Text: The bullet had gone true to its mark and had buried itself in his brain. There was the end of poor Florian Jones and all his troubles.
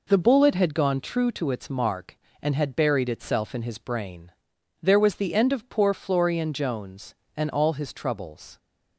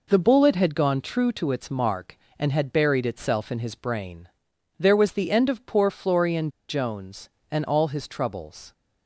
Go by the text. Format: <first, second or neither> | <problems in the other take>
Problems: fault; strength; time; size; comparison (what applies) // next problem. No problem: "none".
first | pauses between "Florian" and "Jones"; slight; at 6.4 s; 0.20 s long